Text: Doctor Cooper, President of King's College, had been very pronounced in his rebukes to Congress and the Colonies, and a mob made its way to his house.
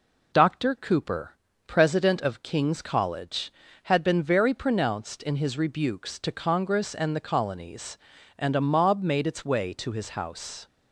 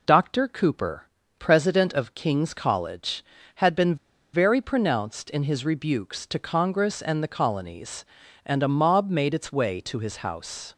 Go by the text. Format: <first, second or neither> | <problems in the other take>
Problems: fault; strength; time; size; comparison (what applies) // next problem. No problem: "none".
first | pauses between "been" and "very"; at 3.9 s; 0.38 s long